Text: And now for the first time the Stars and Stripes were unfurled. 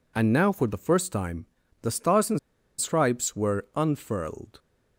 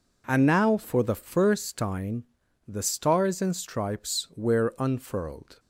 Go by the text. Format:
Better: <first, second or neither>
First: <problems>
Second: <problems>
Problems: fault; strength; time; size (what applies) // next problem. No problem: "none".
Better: second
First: pauses between "time" and "the"; slight; at 1.4 s; 0.36 s long // pauses between "and" and "Stripes"; at 2.3 s; 0.41 s long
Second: pauses between "time" and "the"; at 2.2 s; 0.42 s long